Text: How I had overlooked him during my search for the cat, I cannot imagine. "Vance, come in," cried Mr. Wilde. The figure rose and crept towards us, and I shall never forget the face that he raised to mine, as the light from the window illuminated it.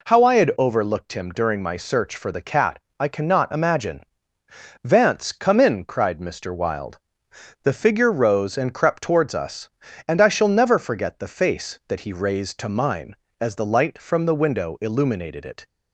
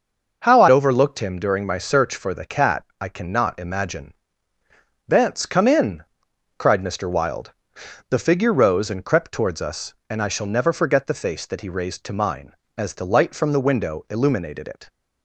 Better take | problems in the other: first | skips "had"; at 0.6 s

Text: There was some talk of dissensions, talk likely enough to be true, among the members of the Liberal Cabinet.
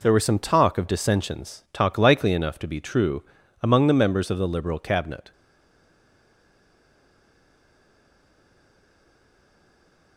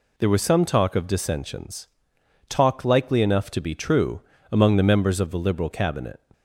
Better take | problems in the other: second | stays silent after the last word; strong; from 5.3 s on; 4.8 s long

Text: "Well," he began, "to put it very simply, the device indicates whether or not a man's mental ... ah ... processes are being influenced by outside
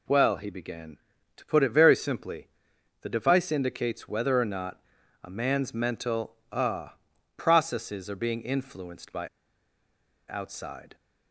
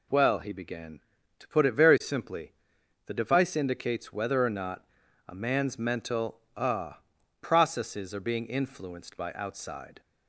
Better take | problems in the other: second | pauses between "not" and "a"; at 4.7 s; 0.44 s long; also in the second // pauses between "by" and "outside"; at 9.2 s; 1.0 s long

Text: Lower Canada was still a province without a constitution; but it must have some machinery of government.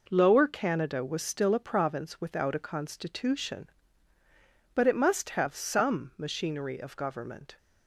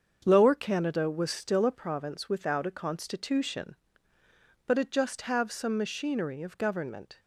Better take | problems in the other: first | starts louder than the rest; until 1.2 s; 7 dB // says "just" for "must"; at 4.8 s

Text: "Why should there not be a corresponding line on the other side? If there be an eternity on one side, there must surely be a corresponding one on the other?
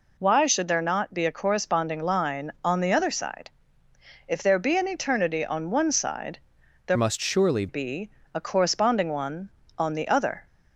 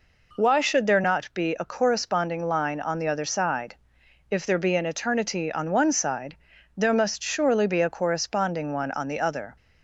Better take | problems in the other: second | changes voice from "must" to "surely"; from 6.9 to 7.6 s; 0.7 s long // pauses between "be" and "a"; slight; at 8.0 s; 0.24 s long

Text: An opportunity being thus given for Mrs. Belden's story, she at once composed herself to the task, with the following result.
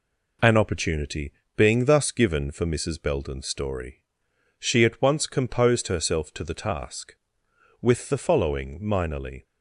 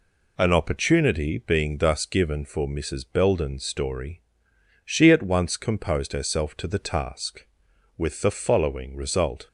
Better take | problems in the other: second | pauses between "opportunity" and "being"; slight; at 1.3 s; 0.24 s long // says "minorly" for "result"; at 8.8 s

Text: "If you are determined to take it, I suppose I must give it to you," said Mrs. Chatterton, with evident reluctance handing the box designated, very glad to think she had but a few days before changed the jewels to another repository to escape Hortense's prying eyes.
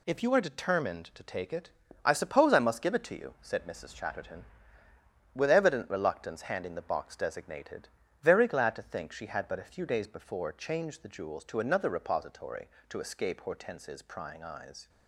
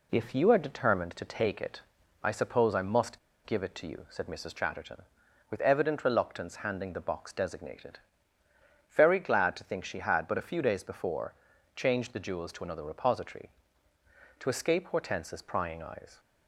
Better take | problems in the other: first | pauses between "must" and "give"; slight; at 3.1 s; 0.27 s long // pauses between "before" and "changed"; at 11.3 s; 0.40 s long

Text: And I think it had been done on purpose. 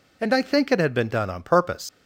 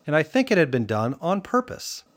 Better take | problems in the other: second | leaves "purpose" unfinished; at 1.8 s; 95 ms

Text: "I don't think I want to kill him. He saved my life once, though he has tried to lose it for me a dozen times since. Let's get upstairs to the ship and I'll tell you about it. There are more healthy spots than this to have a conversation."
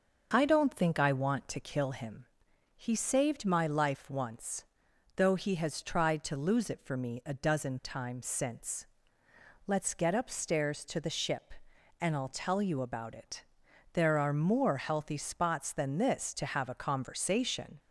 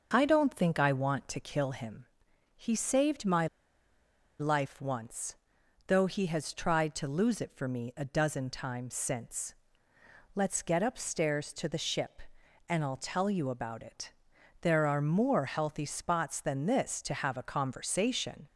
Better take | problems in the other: first | starts louder than the rest; until 1.1 s; 6.5 dB; also in the first // pauses between "my" and "life"; noticeable; at 3.4 s; 0.93 s long

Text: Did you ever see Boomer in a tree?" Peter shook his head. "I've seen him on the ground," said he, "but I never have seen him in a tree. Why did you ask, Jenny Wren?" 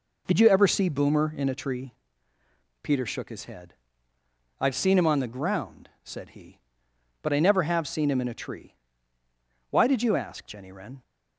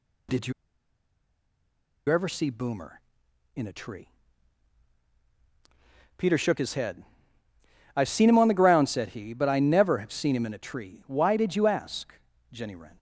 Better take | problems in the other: first | pauses between "you" and "ever"; strong; at 0.5 s; 1.5 s long

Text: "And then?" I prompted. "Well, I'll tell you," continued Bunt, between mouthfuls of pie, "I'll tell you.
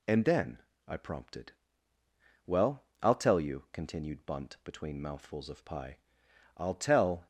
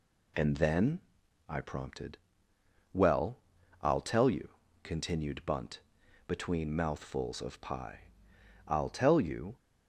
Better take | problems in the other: second | stops before "you"; at 7.2 s

